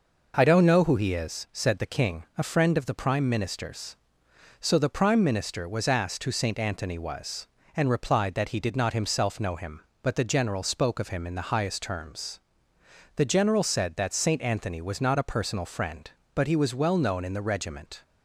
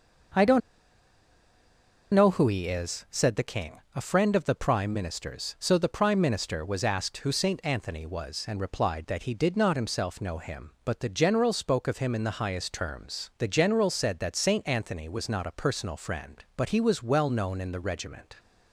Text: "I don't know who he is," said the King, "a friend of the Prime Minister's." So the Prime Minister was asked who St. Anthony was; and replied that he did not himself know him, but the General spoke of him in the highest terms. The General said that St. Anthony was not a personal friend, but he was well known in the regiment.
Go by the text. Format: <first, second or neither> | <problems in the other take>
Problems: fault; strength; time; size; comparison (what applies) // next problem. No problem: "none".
first | pauses between "don't" and "know"; strong; at 0.6 s; 1.5 s long